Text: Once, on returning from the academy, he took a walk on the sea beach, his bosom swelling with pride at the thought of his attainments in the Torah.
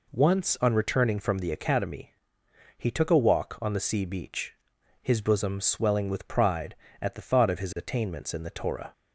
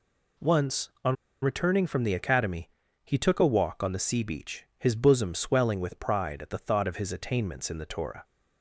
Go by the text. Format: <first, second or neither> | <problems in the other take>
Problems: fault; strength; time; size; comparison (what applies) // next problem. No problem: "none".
first | pauses between "on" and "returning"; slight; at 1.1 s; 0.28 s long